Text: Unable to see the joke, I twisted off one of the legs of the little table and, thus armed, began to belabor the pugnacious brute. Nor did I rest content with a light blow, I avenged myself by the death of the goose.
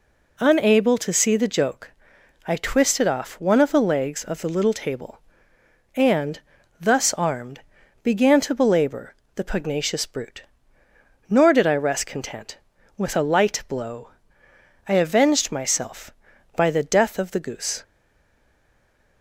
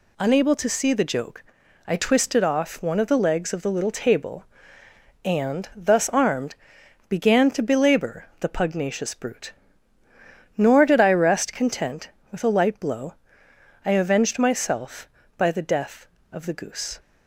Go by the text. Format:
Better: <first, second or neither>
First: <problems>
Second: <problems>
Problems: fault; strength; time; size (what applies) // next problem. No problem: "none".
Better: second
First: pauses between "belabor" and "the"; slight; at 9.1 s; 0.20 s long // stays silent after the last word; noticeable; from 17.8 s on; 1.4 s long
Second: none